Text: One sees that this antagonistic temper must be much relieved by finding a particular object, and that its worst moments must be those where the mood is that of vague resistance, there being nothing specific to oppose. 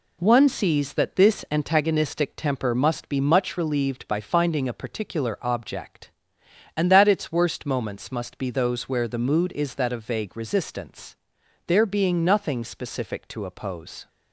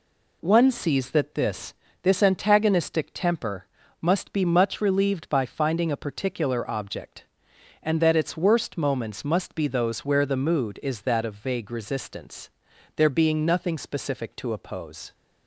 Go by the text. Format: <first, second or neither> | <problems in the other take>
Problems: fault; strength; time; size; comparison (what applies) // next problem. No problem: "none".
first | says "this" twice; at 2.0 s // pauses between "temper" and "must"; slight; at 3.6 s; 0.34 s long